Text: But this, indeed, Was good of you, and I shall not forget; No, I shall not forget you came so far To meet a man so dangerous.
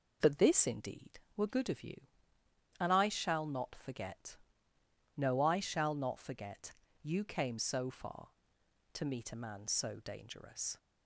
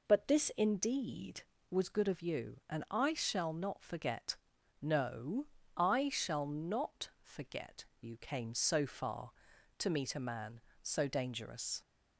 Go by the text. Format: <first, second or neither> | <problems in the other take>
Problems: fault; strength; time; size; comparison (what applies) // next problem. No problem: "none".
second | says "Were" for "Was"; at 1.3 s // pauses between "forget" and "you"; slight; at 6.7 s; 0.28 s long; slight in the second